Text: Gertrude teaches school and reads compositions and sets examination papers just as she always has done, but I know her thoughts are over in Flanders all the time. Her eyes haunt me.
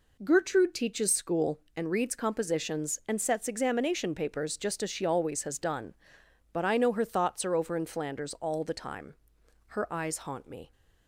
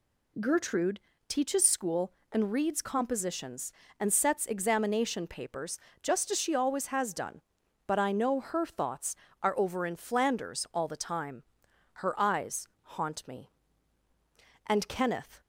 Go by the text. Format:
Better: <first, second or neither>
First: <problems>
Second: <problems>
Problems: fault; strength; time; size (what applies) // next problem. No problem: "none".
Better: first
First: none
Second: pauses between "Gertrude" and "teaches"; slight; at 0.9 s; 0.30 s long // pauses between "papers" and "just"; slight; at 5.7 s; 0.24 s long // pauses between "eyes" and "haunt"; slight; at 12.6 s; 0.16 s long // goes on to say "And Kenneth"; noticeable; from 14.6 s on; 0.74 s long